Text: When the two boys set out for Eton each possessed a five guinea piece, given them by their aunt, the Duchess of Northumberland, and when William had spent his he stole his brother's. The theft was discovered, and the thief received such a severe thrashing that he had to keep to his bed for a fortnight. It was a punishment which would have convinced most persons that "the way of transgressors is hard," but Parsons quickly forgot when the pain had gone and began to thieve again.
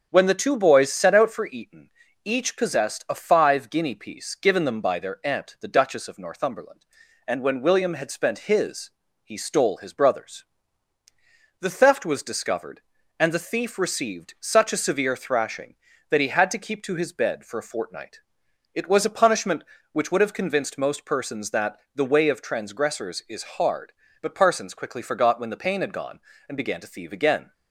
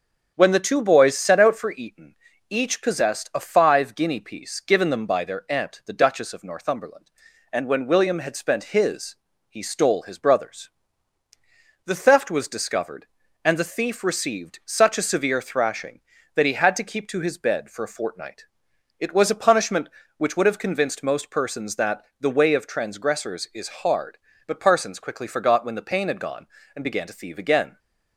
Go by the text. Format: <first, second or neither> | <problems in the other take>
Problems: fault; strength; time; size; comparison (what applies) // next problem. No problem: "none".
neither | starts louder than the rest; the same in both // pauses between "Eton" and "each"; slight; the same in both // pauses between "his" and "he"; slight; the same in both // pauses between "that" and "the"; slight; the same in both